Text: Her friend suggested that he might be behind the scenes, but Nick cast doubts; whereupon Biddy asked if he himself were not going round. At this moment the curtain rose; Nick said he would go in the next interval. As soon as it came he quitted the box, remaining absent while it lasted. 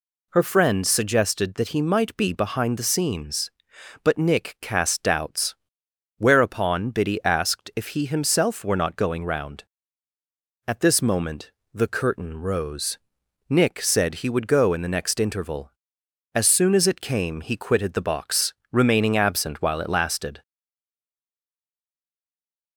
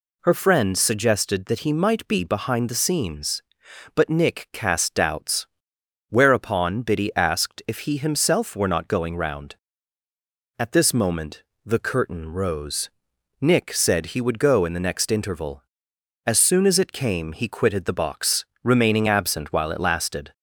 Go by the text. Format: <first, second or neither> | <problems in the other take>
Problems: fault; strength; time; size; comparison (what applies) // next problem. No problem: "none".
second | pauses between "moment" and "the"; slight; at 11.5 s; 0.22 s long; slight in the second // stays silent after the last word; from 20.4 s on; 2.3 s long